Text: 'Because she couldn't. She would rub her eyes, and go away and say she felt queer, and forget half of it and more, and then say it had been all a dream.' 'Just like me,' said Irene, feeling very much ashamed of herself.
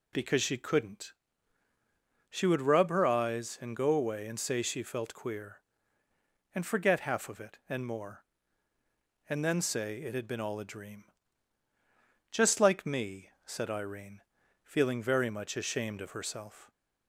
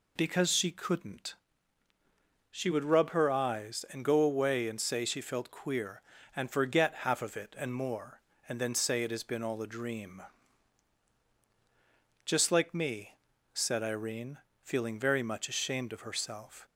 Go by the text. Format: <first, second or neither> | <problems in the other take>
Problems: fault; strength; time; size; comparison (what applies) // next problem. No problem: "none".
first | says "has" for "had"; at 9.1 s